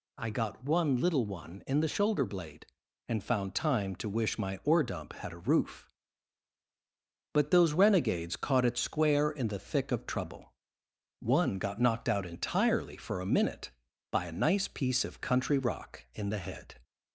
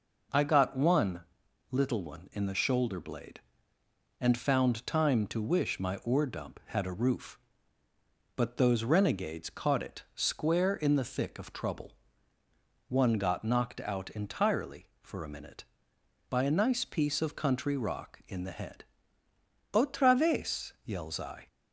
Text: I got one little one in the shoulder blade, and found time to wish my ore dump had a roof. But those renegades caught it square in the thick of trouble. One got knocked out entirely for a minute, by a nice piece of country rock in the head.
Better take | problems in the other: first | pauses between "one" and "little"; noticeable; at 1.2 s; 0.48 s long // goes on to say "Otra vez yells I"; strong; from 19.7 s on; 1.7 s long

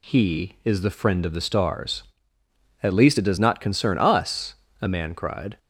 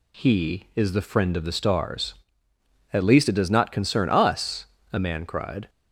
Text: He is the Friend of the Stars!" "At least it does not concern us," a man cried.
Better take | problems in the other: neither | none

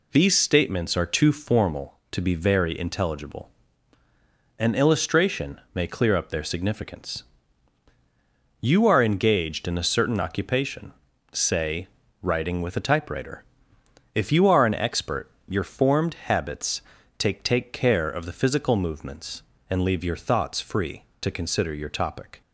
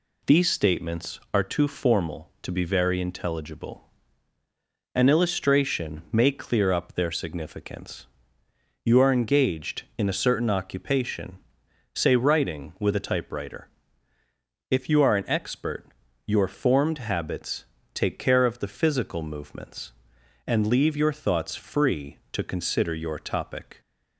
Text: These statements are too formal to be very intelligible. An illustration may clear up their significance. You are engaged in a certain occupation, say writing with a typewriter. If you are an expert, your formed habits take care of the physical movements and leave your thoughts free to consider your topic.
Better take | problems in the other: second | pauses between "illustration" and "may"; slight; at 5.5 s; 0.16 s long // pauses between "say" and "writing"; slight; at 11.8 s; 0.34 s long // pauses between "habits" and "take"; at 16.8 s; 0.38 s long; slight in the second // says "take" twice; at 17.4 s

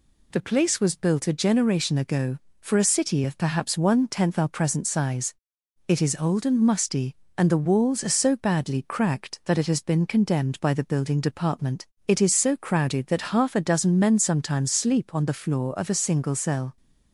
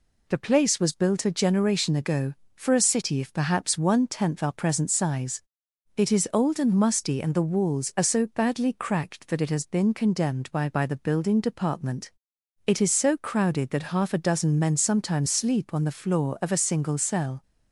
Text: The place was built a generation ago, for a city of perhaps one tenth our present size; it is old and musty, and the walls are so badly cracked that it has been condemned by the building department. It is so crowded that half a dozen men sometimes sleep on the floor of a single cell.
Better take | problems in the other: first | says "by" twice; at 10.6 s

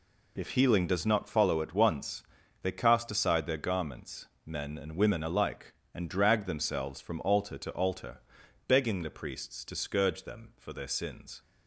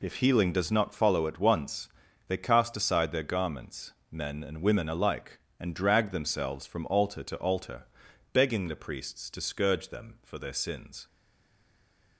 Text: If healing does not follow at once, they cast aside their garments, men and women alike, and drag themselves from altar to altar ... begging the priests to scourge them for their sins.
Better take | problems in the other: first | stays silent after the last word; from 11.0 s on; 1.1 s long

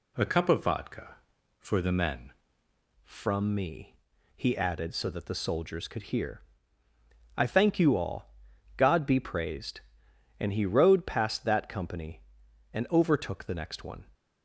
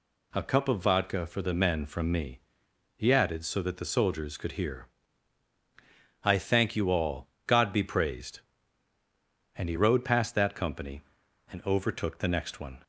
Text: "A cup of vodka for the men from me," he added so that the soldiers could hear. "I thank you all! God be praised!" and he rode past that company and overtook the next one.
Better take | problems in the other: second | changes voice at "from"; from 3.0 s on; 11.0 s long

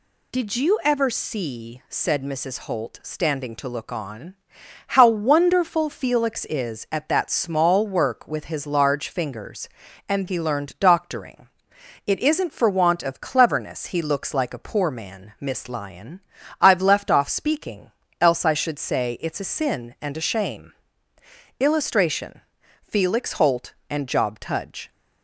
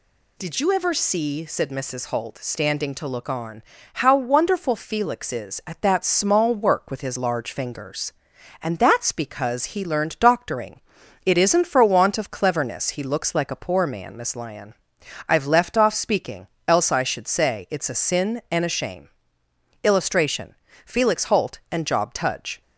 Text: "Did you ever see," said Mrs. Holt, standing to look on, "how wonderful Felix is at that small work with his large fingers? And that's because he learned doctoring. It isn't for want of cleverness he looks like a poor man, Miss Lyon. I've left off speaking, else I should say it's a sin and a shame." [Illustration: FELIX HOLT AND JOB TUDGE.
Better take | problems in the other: second | skips "that's because"; at 10.2 s

